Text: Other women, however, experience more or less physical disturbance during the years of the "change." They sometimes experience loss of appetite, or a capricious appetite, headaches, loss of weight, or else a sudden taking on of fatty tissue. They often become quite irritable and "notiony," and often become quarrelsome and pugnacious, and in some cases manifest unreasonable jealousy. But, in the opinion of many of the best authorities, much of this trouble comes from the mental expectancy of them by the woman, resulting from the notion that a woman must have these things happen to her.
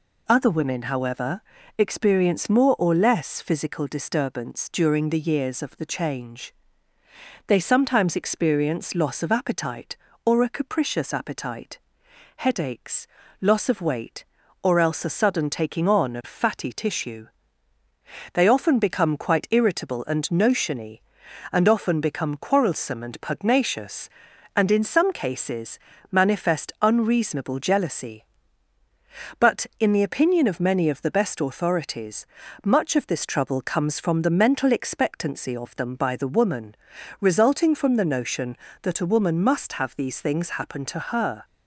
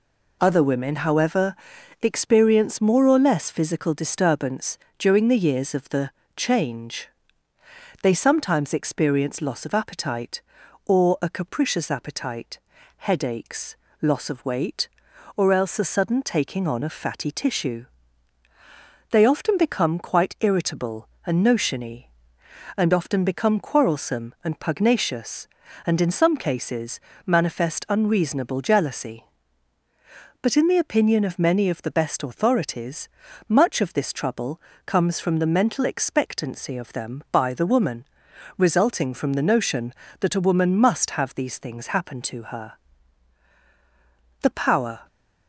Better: first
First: pauses between "cases" and "manifest"; slight; at 25.7 s; 0.32 s long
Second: pauses between "disturbance" and "during"; slight; at 4.7 s; 0.18 s long // pauses between "the" and "change"; slight; at 6.1 s; 0.26 s long // pauses between "cases" and "manifest"; slight; at 26.9 s; 0.26 s long // pauses between "trouble" and "comes"; slight; at 34.6 s; 0.24 s long // goes on to say "The power"; noticeable; from 44.4 s on; 0.64 s long

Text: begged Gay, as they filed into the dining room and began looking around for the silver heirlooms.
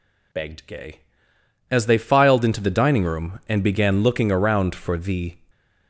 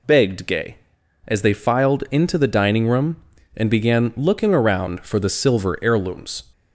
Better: second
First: stops before "silver heirlooms"; at 5.5 s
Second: none

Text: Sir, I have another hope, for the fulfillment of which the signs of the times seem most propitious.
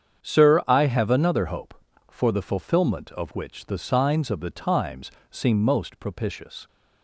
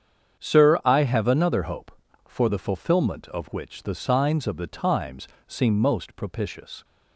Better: neither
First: starts louder than the rest; strong; until 1.2 s; 8 dB // pauses between "times" and "seem"; slight; at 5.1 s; 0.18 s long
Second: starts louder than the rest; strong; until 1.4 s; 8 dB // pauses between "times" and "seem"; slight; at 5.2 s; 0.18 s long

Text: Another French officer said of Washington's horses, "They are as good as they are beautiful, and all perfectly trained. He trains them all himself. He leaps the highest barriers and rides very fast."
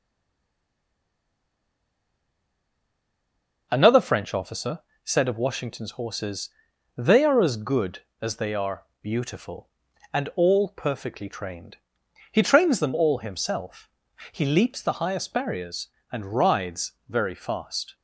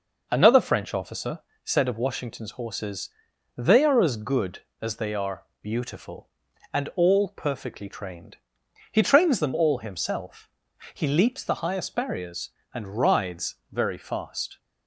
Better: second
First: stays silent before the first word; strong; until 3.7 s; 3.7 s long // pauses between "officer" and "said"; slight; at 4.8 s; 0.24 s long // pauses between "are" and "beautiful"; slight; at 8.8 s; 0.18 s long // pauses between "rides" and "very"; slight; at 16.9 s; 0.18 s long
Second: pauses between "officer" and "said"; slight; at 1.4 s; 0.24 s long // pauses between "are" and "beautiful"; slight; at 5.4 s; 0.18 s long // pauses between "rides" and "very"; slight; at 13.5 s; 0.18 s long

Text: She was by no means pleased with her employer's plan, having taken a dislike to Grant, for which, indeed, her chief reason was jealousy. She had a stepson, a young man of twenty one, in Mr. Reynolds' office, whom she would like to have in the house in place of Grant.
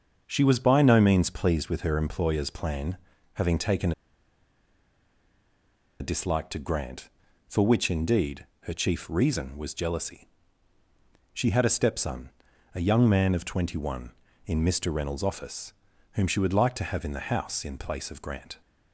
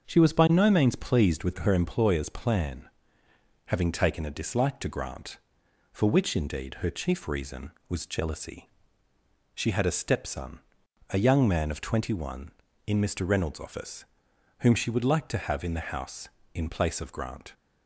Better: second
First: starts louder than the rest; until 1.2 s; 7 dB // pauses between "taken" and "a"; strong; at 3.9 s; 2.0 s long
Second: starts louder than the rest; until 1.0 s; 6.5 dB

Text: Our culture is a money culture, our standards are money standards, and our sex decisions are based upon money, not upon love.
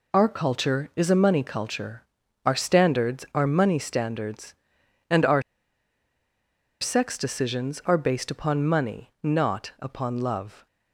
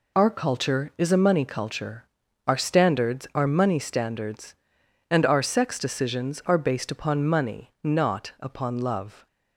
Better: second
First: pauses between "our" and "sex"; strong; at 5.4 s; 1.3 s long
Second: none

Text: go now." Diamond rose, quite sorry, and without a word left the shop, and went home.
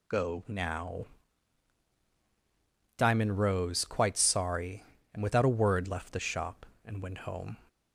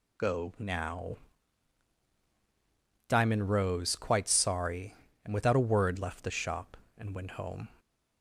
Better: neither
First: none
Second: none

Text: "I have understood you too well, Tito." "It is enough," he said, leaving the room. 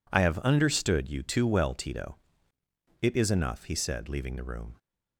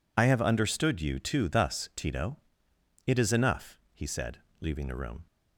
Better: first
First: none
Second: says "thus" for "well"; at 1.4 s

